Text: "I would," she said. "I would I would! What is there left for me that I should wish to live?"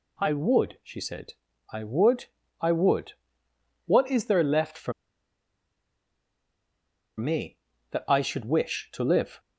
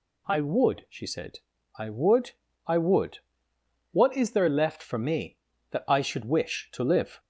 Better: second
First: pauses between "would" and "I"; slight; at 2.2 s; 0.34 s long // pauses between "for" and "me"; strong; at 4.9 s; 2.2 s long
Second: pauses between "would" and "I"; slight; at 2.3 s; 0.34 s long

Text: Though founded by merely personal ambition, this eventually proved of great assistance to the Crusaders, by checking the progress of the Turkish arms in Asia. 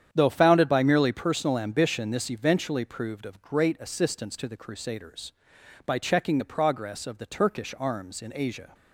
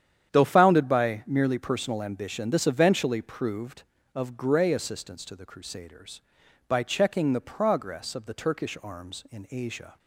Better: first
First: starts louder than the rest; strong; until 1.1 s; 9 dB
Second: starts louder than the rest; strong; until 1.3 s; 9 dB // says "grey" for "great"; at 4.3 s

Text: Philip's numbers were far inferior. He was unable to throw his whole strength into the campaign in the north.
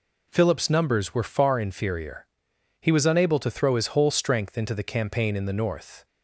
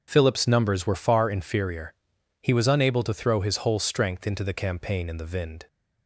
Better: first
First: none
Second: starts louder than the rest; until 1.0 s; 6.5 dB // says "vind" for "north"; at 5.3 s

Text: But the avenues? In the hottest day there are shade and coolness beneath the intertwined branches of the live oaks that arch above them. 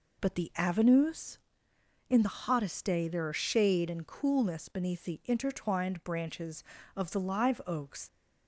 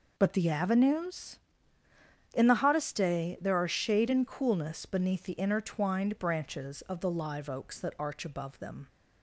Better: second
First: stops before "that arch above them"; at 8.0 s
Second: none

